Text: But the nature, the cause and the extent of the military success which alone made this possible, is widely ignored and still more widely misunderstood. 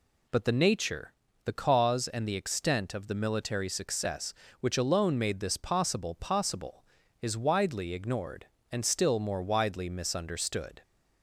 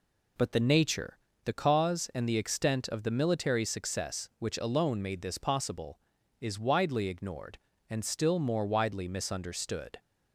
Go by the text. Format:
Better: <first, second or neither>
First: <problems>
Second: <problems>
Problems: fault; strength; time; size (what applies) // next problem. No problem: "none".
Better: second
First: says "possible" twice; at 6.1 s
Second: none